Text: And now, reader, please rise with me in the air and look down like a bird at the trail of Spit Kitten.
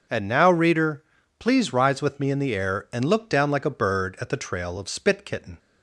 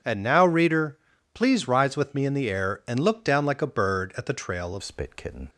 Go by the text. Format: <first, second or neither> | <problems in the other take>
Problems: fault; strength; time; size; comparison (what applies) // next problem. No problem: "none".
first | starts louder than the rest; strong; until 1.4 s; 8 dB; also in the first // changes voice at "Spit"; from 4.8 s on; 0.6 s long